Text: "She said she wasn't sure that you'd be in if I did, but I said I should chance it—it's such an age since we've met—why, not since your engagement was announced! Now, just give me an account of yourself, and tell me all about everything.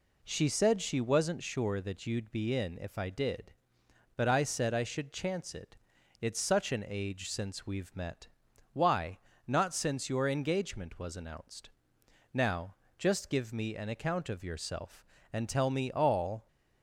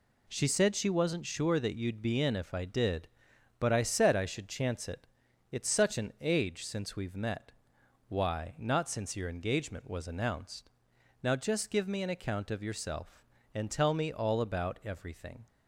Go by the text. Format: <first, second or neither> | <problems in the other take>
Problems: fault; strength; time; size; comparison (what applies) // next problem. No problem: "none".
second | stops before "about everything"; at 16.4 s